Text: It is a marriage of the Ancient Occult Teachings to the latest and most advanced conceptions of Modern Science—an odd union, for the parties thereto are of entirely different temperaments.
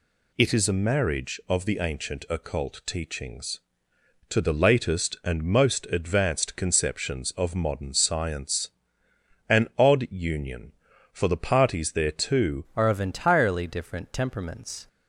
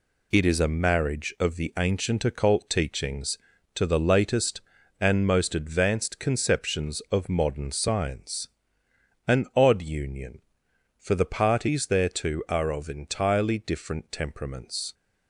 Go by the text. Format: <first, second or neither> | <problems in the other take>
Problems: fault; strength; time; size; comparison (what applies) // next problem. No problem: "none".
second | changes voice at "are"; from 12.7 s on; 2.1 s long